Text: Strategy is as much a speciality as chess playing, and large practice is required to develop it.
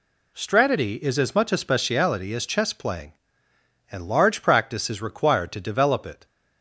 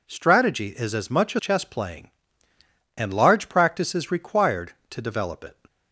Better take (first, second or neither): first